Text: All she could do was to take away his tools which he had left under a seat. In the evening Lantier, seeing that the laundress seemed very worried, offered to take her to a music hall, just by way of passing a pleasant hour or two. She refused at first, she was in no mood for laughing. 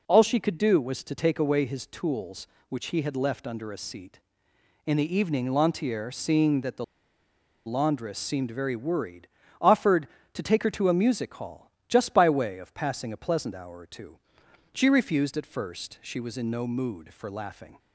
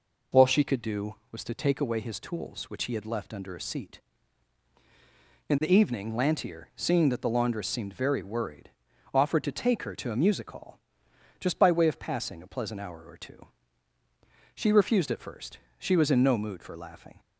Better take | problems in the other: second | pauses between "the" and "laundress"; noticeable; at 6.8 s; 0.81 s long

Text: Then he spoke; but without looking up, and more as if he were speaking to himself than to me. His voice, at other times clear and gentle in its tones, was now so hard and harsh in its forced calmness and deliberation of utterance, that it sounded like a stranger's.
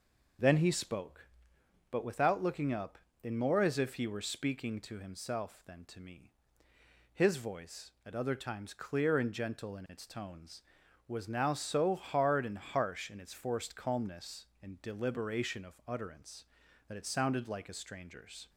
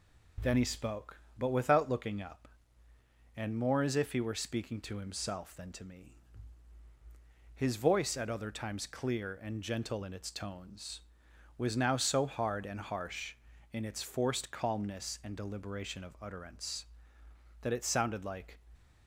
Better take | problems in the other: first | stops before "a stranger's"; at 18.7 s

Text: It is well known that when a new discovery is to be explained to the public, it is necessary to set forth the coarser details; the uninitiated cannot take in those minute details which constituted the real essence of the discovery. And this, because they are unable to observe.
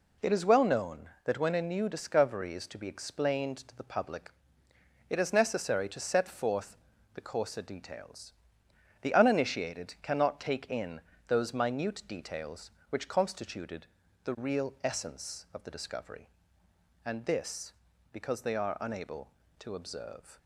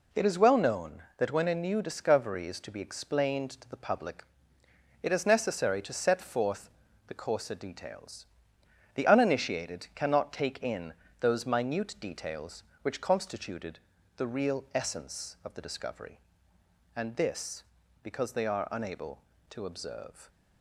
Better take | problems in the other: neither | pauses between "forth" and "the"; the same in both // pauses between "in" and "those"; slight; the same in both // pauses between "constituted" and "the"; the same in both

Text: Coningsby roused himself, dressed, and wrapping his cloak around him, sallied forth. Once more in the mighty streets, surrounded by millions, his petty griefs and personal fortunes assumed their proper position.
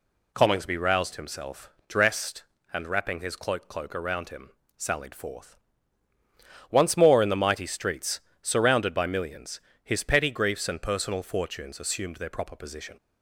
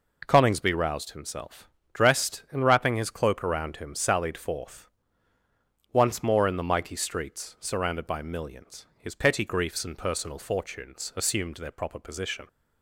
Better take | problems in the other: second | says "cloak" twice; at 3.6 s

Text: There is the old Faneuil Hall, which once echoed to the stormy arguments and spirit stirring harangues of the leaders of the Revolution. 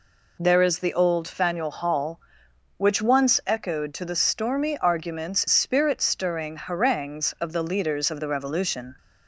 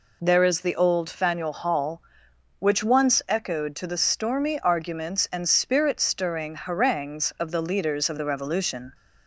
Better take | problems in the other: second | skips "and"; at 5.4 s

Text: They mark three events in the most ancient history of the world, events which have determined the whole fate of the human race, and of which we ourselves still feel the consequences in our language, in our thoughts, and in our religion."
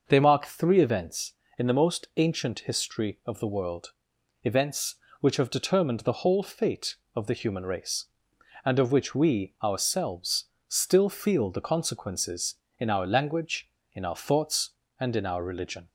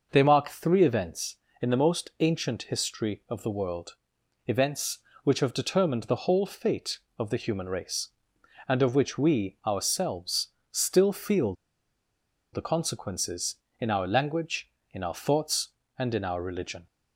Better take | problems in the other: first | pauses between "ourselves" and "still"; slight; at 10.4 s; 0.22 s long; slight in the first // pauses between "feel" and "the"; at 11.5 s; 1.0 s long

